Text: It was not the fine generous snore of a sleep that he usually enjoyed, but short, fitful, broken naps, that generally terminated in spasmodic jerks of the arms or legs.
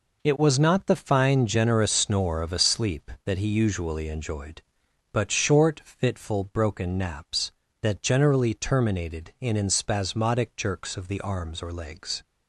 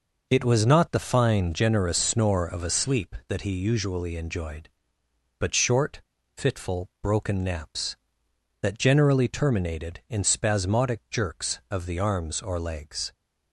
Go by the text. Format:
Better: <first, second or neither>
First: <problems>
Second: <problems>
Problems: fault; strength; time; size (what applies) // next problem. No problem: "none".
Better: second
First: says "in" twice; at 9.5 s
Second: none